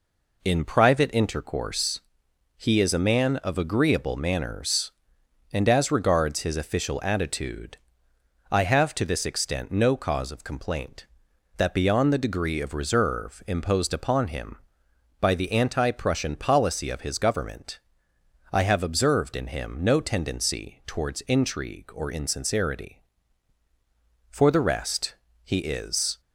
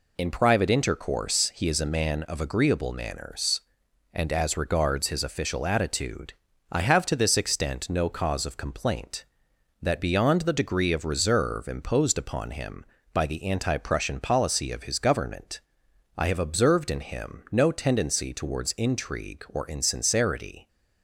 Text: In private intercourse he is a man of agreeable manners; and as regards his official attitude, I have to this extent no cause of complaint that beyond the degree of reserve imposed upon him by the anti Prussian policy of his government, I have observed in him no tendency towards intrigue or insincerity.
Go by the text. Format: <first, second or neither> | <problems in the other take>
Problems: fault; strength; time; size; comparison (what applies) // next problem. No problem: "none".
second | pauses between "intercourse" and "he"; noticeable; at 1.9 s; 0.56 s long // goes on to say "For the rest he is"; strong; from 24.2 s on; 1.9 s long